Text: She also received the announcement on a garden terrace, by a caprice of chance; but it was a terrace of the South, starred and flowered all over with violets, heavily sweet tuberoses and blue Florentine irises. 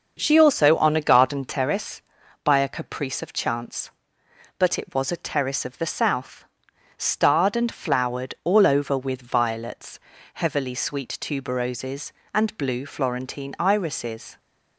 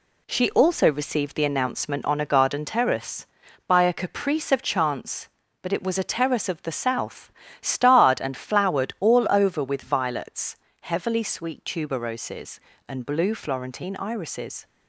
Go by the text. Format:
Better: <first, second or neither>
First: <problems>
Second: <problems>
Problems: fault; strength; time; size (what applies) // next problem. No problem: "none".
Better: second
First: starts louder than the rest; until 1.2 s; 6 dB // skips "received the announcement"; at 0.7 s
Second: none